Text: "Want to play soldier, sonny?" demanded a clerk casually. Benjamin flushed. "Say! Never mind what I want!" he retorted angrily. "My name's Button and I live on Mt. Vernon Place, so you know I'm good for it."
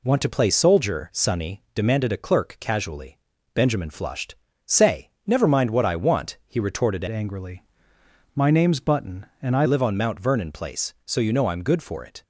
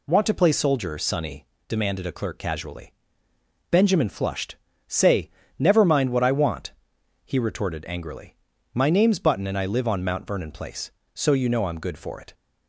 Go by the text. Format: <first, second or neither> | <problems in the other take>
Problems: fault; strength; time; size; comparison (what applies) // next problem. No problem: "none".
second | changes voice from "angrily" to "I"; from 7.0 to 9.6 s; 2.6 s long